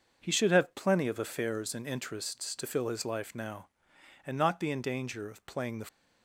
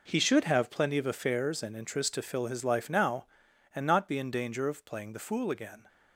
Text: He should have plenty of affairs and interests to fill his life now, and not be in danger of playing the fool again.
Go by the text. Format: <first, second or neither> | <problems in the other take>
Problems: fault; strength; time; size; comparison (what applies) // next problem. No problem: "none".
second | starts louder than the rest; until 1.2 s; 6.5 dB // stops before "fool again"; at 5.8 s